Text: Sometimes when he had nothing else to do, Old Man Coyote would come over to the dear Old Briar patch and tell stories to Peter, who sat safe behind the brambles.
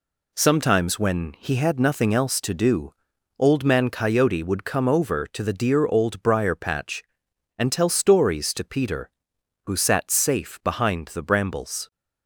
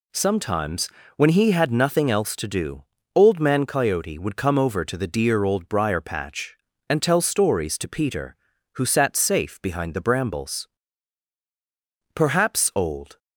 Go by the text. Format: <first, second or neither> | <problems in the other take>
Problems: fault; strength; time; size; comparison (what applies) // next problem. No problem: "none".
first | pauses between "Sometimes" and "when"; slight; at 0.8 s; 0.28 s long // goes on to say "Perhaps Old"; noticeable; from 12.1 s on; 1.0 s long